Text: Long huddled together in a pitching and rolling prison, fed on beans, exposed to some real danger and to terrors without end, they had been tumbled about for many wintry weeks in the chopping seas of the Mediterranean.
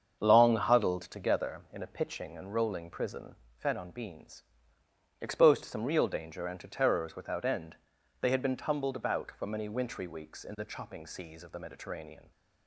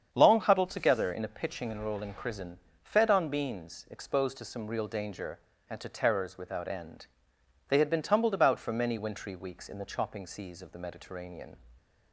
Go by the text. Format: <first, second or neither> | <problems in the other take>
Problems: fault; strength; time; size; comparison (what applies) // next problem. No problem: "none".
neither | starts louder than the rest; the same in both